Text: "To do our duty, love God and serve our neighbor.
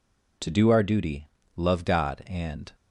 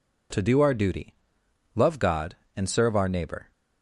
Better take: second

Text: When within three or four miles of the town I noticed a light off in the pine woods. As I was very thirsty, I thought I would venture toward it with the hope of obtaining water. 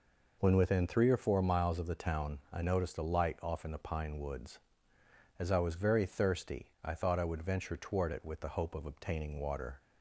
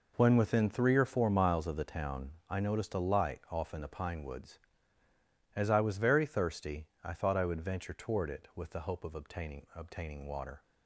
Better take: first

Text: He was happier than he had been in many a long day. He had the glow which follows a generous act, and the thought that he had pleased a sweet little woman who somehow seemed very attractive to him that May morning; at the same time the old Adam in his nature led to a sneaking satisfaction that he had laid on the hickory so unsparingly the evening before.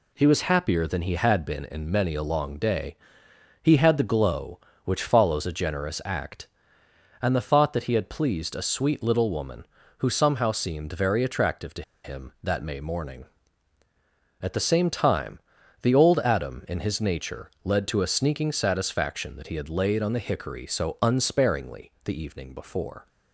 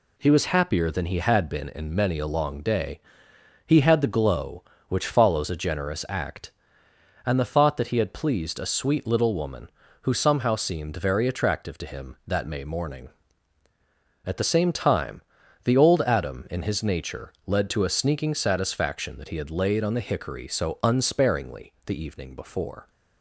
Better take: second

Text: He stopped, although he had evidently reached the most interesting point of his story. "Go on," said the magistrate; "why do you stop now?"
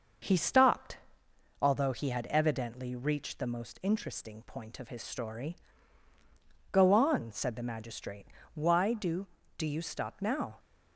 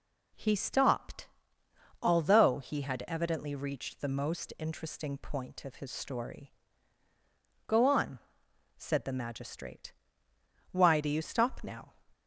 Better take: second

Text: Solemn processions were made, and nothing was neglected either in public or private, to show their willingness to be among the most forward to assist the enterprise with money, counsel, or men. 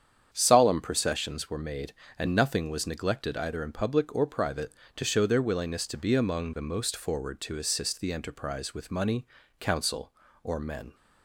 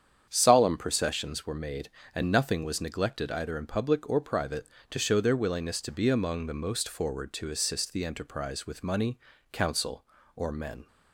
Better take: neither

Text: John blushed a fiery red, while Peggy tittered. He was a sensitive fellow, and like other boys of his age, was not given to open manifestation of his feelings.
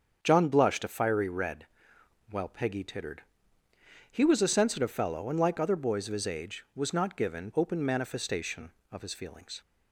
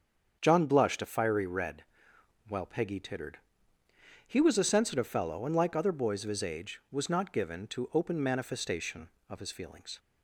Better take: second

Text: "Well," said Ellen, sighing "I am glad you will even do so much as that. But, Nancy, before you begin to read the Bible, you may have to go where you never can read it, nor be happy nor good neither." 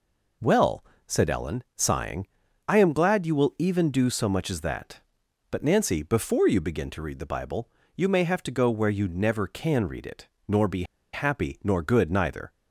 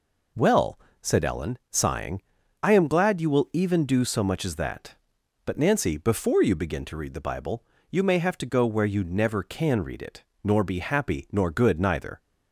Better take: second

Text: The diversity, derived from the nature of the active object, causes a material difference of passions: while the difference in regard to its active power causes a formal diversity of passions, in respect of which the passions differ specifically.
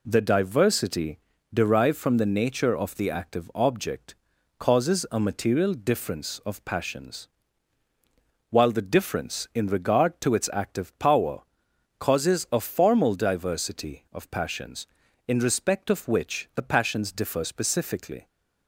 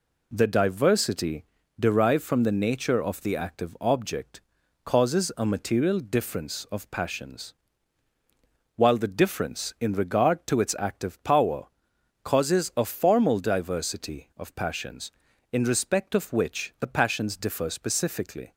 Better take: neither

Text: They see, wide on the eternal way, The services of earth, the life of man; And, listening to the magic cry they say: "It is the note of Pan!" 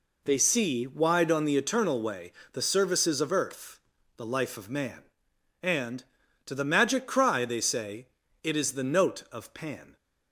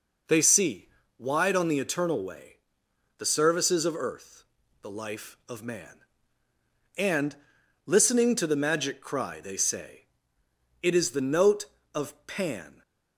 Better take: second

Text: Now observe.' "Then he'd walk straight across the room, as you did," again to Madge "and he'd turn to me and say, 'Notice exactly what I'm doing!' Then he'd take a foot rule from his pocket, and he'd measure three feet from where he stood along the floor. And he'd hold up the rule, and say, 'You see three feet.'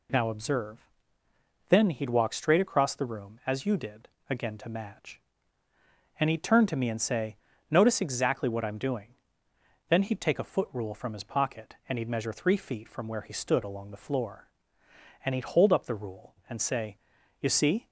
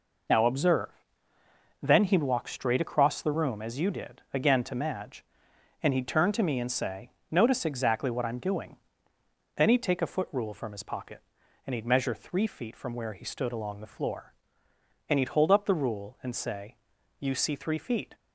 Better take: second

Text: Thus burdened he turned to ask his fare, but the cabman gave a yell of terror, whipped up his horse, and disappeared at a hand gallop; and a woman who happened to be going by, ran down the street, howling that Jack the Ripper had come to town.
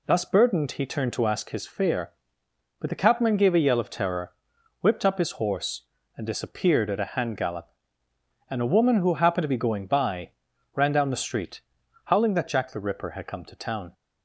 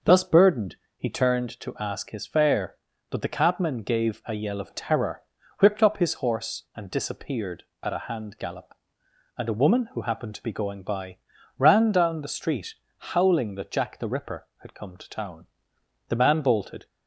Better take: first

